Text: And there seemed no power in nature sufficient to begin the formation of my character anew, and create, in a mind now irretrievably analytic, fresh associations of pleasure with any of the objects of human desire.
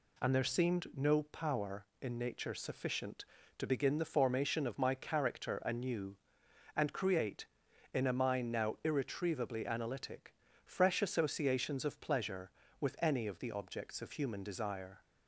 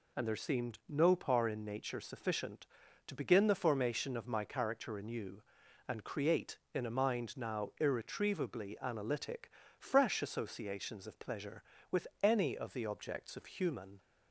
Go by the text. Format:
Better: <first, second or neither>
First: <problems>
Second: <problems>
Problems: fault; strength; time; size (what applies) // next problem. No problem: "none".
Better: first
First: none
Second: stops before "desire"; at 13.9 s